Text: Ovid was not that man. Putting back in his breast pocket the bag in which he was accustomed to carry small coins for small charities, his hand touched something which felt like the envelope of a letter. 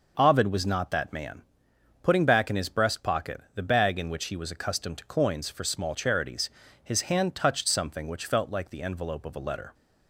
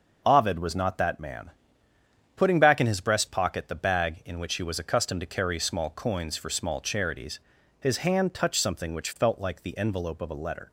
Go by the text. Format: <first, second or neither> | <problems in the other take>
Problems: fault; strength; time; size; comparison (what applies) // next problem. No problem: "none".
second | skips "carry small"; at 5.0 s